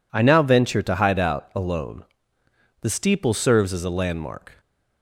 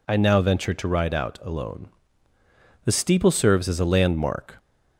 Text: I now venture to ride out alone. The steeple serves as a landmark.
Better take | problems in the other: second | says "hide" for "ride"; at 0.9 s

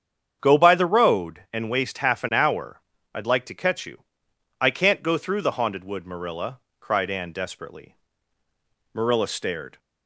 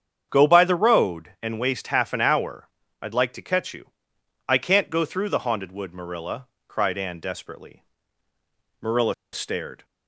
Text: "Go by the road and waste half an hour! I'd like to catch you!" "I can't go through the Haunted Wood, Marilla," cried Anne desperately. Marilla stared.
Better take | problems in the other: first | starts louder than the rest; strong; until 1.3 s; 8 dB; strong in the first // pauses between "Marilla" and "stared"; slight; at 9.1 s; 0.20 s long

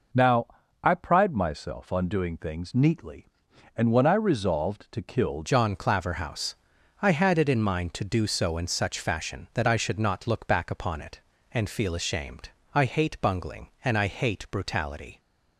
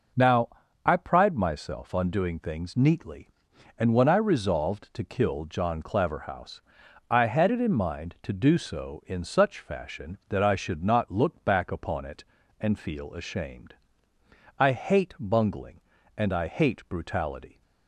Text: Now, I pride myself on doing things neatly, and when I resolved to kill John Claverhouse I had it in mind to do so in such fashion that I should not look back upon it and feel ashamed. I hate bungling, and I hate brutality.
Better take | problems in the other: second | changes voice at "John"; from 5.4 s on; 9.7 s long // pauses between "Claverhouse" and "I"; noticeable; at 6.5 s; 0.48 s long; noticeable in the second

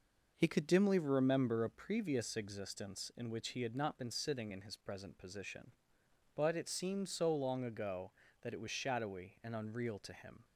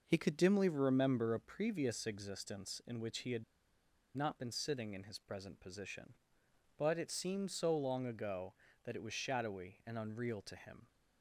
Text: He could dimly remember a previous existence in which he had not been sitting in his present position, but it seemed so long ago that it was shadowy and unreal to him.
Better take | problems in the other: first | pauses between "had" and "not"; noticeable; at 3.4 s; 0.73 s long

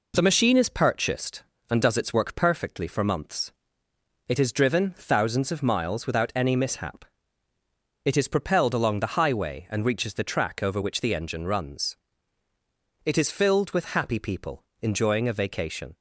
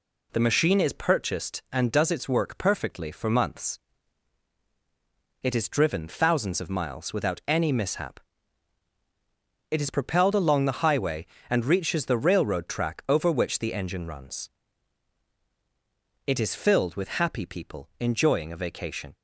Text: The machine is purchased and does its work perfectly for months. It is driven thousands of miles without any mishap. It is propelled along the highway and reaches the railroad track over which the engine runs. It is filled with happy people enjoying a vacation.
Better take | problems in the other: second | skips "railroad"; at 10.2 s // pauses between "people" and "enjoying"; slight; at 14.6 s; 0.20 s long

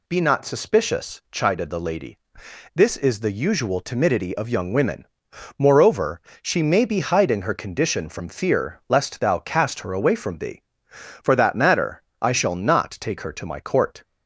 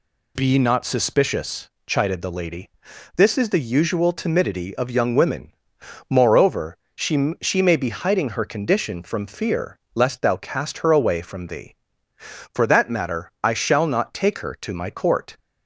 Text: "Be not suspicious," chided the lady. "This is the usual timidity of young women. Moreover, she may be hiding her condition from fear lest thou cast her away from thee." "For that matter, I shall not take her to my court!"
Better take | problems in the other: first | says "she" twice; at 7.4 s // pauses between "fear" and "lest"; slight; at 9.7 s; 0.16 s long

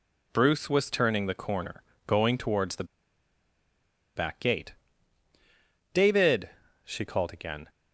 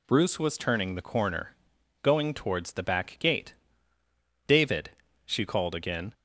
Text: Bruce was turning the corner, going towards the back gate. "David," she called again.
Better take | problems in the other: second | pauses between "the" and "back"; strong; at 2.8 s; 1.3 s long

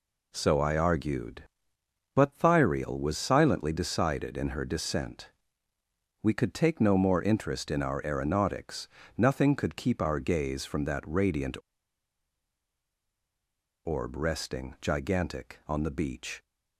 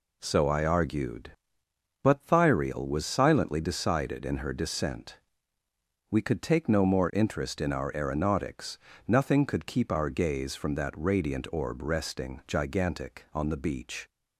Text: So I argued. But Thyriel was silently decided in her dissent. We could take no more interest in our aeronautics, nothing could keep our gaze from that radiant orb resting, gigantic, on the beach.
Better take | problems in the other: second | pauses between "radiant" and "orb"; strong; at 11.5 s; 2.2 s long

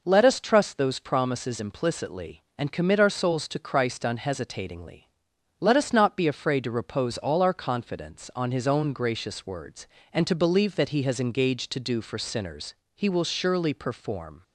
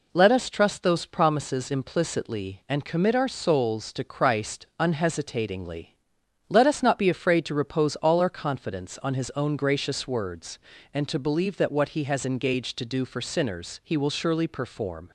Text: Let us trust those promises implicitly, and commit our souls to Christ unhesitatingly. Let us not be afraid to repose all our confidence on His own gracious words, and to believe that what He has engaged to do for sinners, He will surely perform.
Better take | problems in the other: second | skips "what"; at 10.8 s

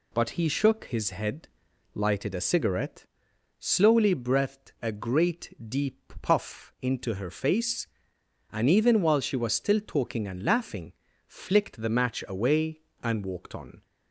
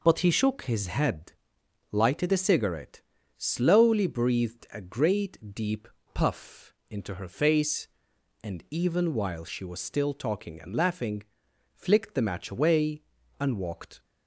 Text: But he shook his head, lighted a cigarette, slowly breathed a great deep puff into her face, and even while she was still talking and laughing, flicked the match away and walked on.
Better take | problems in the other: first | pauses between "deep" and "puff"; slight; at 5.8 s; 0.26 s long // pauses between "puff" and "into"; slight; at 6.7 s; 0.16 s long // stops before "on"; at 14.0 s

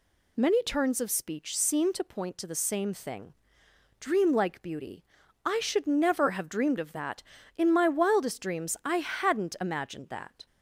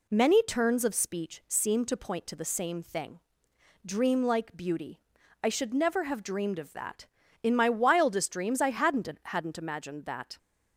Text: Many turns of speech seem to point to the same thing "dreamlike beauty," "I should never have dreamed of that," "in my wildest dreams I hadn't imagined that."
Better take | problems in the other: first | pauses between "thing" and "dreamlike"; noticeable; at 3.1 s; 0.64 s long; noticeable in the first // says "hadn't" twice; at 9.2 s

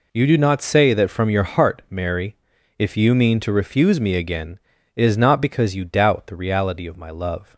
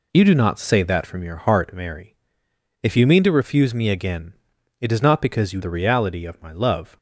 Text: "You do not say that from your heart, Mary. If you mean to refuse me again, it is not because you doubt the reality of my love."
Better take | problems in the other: first | skips "doubt"; at 5.6 s

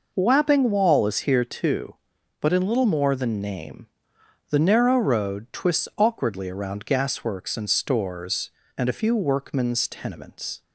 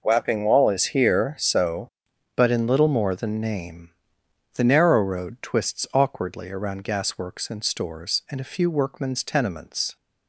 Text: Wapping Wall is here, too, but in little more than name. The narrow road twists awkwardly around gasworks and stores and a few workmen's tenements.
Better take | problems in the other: first | says "so" for "too"; at 1.3 s

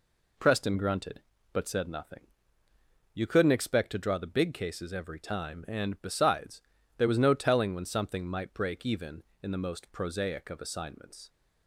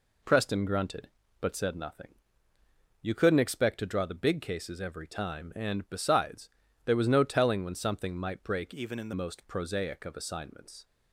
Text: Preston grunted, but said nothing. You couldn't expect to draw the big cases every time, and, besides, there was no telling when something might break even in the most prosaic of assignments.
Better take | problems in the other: first | changes voice from "even" to "the"; from 8.7 to 9.1 s; 0.4 s long

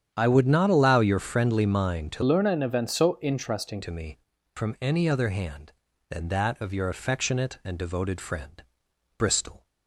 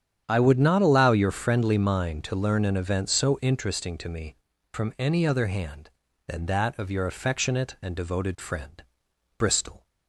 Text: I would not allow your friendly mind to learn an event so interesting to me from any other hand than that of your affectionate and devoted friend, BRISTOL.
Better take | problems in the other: second | starts louder than the rest; strong; until 1.1 s; 8.5 dB; strong in the second // changes voice from "learn" to "interesting"; from 2.2 to 3.8 s; 1.6 s long

